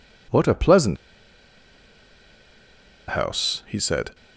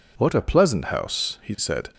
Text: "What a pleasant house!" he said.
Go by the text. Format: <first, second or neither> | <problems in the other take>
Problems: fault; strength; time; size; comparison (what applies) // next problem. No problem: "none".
second | pauses between "pleasant" and "house"; strong; at 0.9 s; 2.1 s long